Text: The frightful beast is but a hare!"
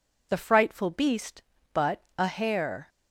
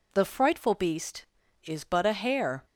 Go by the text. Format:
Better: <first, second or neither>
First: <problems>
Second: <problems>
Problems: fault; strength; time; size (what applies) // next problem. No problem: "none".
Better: second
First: skips "is"; at 1.5 s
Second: none